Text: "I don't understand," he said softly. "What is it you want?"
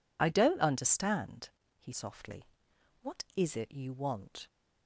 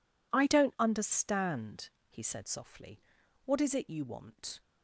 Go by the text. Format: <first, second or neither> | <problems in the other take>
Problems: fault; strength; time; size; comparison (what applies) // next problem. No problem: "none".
second | skips "said"; at 1.9 s